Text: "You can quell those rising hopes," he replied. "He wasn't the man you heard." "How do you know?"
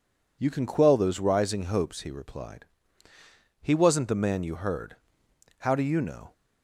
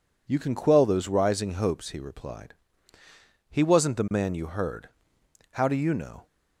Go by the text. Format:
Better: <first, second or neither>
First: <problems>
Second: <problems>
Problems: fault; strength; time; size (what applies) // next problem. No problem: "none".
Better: neither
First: none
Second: none